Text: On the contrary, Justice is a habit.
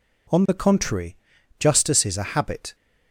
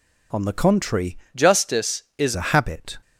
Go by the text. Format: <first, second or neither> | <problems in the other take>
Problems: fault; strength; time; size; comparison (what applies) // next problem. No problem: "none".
first | changes voice from "Justice" to "is"; from 1.3 to 2.3 s; 1.0 s long